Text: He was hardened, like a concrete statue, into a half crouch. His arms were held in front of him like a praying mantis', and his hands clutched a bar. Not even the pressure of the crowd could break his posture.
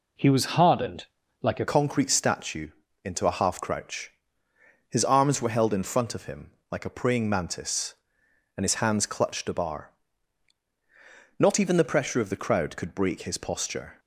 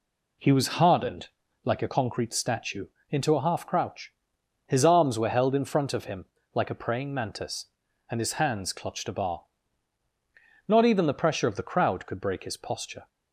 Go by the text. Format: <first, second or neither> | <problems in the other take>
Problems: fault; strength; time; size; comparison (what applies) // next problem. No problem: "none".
second | changes voice at "concrete"; from 1.6 s on; 12.3 s long // pauses between "him" and "like"; slight; at 6.5 s; 0.20 s long; slight in the second